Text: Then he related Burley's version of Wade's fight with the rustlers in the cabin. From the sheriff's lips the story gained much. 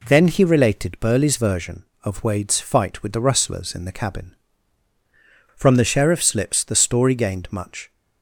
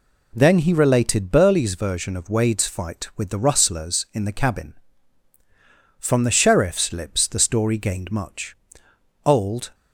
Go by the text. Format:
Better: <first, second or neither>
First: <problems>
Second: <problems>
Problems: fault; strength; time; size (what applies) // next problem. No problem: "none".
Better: first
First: none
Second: goes on to say "Old"; from 9.2 s on; 0.50 s long